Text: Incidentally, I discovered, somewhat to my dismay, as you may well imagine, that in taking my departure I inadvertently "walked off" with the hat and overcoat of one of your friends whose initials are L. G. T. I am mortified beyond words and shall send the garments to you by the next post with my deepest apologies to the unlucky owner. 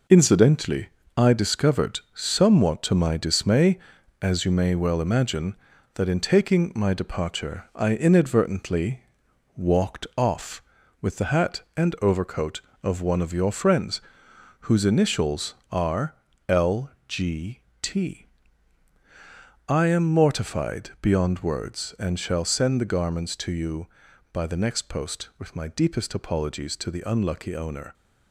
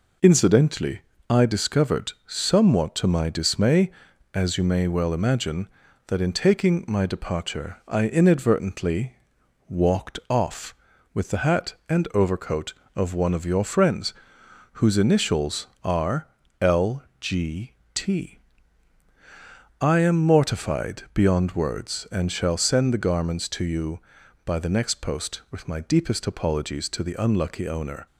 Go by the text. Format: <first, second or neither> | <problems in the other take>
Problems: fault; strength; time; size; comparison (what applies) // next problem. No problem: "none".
second | gets quieter; throughout; 6.5 dB // pauses between "inadvertently" and "walked"; noticeable; at 9.0 s; 0.52 s long; noticeable in the second // pauses between "friends" and "whose"; noticeable; at 14.0 s; 0.60 s long; noticeable in the second // pauses between "are" and "L"; slight; at 16.1 s; 0.34 s long; slight in the second // pauses between "L" and "G"; slight; at 16.8 s; 0.18 s long; slight in the second // pauses between "G" and "T"; slight; at 17.6 s; 0.20 s long; slight in the second // pauses between "T" and "I"; strong; at 18.2 s; 1.4 s long; strong in the second